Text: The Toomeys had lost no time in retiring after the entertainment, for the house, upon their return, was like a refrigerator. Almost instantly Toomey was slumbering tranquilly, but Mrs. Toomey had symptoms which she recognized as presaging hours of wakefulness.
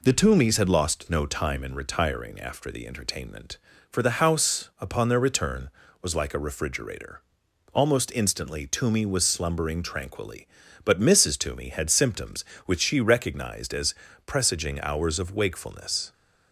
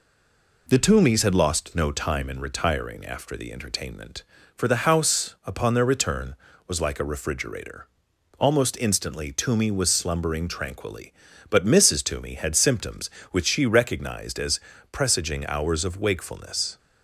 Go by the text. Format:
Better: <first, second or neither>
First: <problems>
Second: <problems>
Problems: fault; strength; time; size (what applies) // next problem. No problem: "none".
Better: first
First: pauses between "as" and "presaging"; slight; at 13.9 s; 0.32 s long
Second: stays silent before the first word; slight; until 0.6 s; 0.6 s long // pauses between "as" and "presaging"; slight; at 14.5 s; 0.32 s long